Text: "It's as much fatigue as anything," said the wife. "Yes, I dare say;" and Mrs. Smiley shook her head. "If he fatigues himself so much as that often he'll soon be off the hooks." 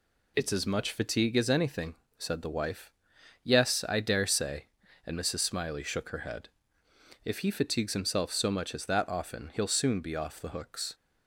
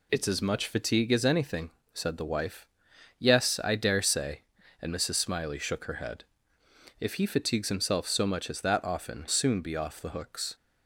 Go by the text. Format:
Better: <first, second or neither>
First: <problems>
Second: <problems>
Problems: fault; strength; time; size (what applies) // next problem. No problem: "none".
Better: first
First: none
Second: skips "he'll"; at 9.2 s